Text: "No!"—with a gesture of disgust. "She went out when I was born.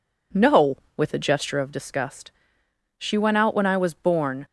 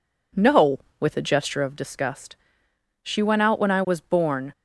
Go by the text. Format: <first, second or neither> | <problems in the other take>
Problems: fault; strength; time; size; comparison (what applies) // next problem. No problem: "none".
neither | none